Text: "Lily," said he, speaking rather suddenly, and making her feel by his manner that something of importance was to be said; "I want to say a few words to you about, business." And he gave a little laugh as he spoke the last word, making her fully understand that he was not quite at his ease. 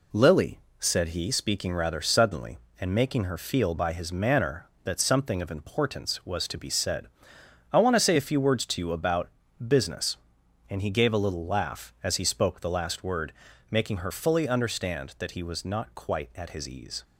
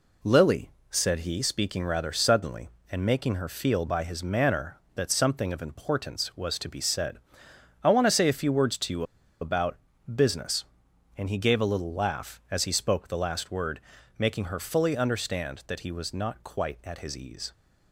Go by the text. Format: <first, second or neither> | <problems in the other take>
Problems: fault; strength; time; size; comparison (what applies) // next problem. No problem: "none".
first | pauses between "you" and "about"; at 9.0 s; 0.36 s long